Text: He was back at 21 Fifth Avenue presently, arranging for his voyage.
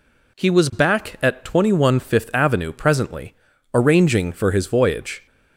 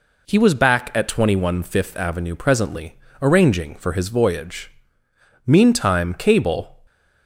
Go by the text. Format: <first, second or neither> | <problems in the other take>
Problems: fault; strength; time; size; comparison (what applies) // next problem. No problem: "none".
first | goes on to say "Meantime cable"; from 5.4 s on; 1.3 s long